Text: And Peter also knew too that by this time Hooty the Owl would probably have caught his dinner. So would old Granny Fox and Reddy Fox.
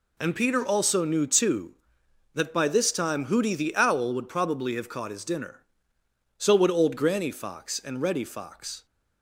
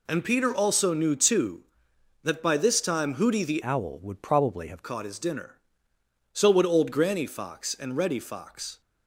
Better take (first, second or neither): first